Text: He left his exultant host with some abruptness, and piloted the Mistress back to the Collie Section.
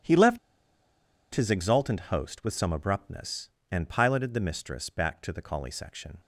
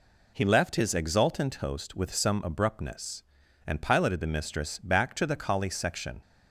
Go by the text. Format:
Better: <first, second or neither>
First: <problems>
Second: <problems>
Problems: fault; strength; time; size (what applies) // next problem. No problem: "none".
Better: second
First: pauses between "left" and "his"; noticeable; at 0.3 s; 0.96 s long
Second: none